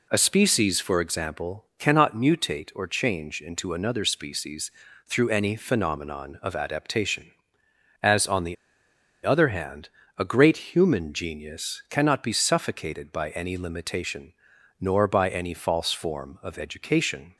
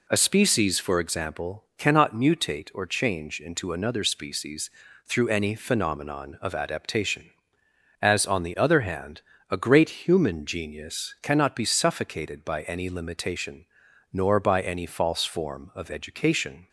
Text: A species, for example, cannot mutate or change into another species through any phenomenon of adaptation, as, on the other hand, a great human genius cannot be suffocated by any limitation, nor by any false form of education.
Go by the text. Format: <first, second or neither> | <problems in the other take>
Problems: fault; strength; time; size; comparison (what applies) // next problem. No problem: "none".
second | pauses between "species" and "through"; slight; at 4.7 s; 0.36 s long; slight in the second // pauses between "the" and "other"; noticeable; at 8.5 s; 0.68 s long